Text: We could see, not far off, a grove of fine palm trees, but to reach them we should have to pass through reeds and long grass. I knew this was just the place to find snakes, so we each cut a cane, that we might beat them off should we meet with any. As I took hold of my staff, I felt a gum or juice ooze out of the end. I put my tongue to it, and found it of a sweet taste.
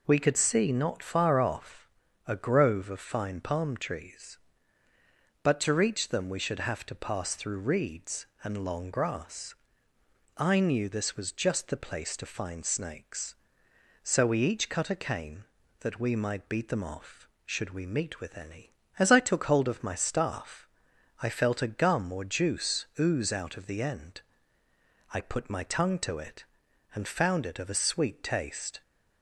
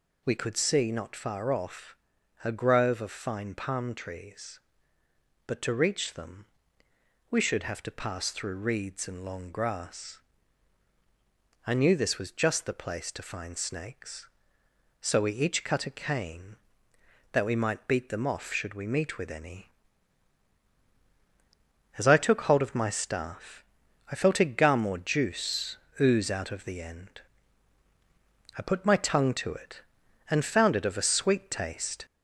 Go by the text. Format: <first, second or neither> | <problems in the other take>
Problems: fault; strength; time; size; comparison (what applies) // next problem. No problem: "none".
first | gets louder; slight; throughout; 3 dB // pauses between "them" and "we"; noticeable; at 6.4 s; 0.86 s long // pauses between "juice" and "ooze"; slight; at 25.7 s; 0.24 s long